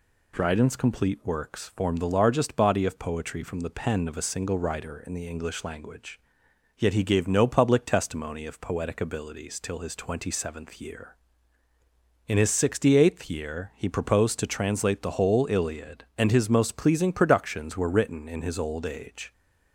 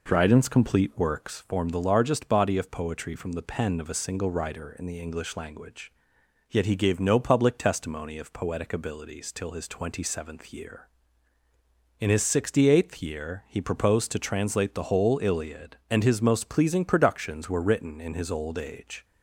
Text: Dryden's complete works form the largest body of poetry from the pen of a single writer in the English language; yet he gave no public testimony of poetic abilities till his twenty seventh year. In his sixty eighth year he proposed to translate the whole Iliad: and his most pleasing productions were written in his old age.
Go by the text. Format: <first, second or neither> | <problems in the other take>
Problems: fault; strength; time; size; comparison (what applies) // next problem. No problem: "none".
first | starts louder than the rest; noticeable; until 1.4 s; 4.5 dB